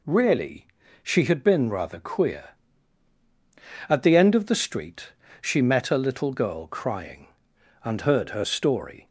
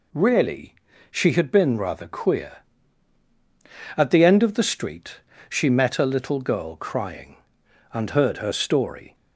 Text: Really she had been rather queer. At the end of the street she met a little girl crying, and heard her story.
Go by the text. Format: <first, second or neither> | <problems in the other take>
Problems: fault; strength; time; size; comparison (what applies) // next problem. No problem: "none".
neither | pauses between "Really" and "she"; slight; the same in both // pauses between "street" and "she"; slight; the same in both